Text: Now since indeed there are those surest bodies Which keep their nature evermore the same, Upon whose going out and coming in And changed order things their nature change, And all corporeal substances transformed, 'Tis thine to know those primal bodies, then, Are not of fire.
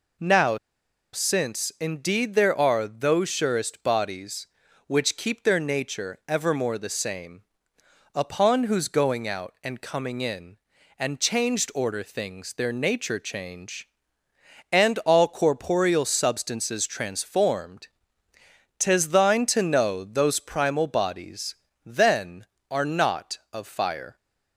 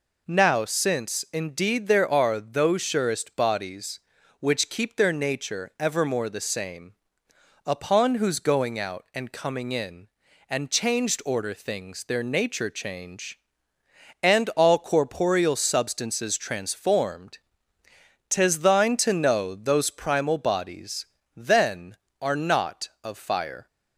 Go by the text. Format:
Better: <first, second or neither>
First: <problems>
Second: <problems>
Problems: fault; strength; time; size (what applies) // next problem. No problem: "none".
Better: second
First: pauses between "Now" and "since"; noticeable; at 0.5 s; 0.56 s long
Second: none